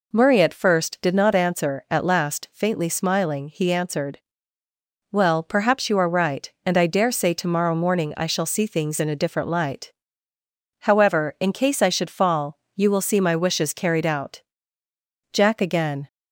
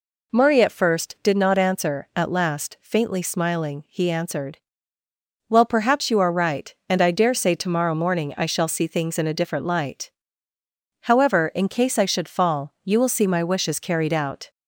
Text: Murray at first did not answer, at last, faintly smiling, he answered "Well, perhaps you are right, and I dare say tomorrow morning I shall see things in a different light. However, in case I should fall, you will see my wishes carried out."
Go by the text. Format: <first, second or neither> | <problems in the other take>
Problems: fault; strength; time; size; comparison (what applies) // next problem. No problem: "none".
second | pauses between "answered" and "Well"; noticeable; at 4.1 s; 0.94 s long; noticeable in the second // goes on to say "Jack again"; noticeable; from 15.3 s on; 0.76 s long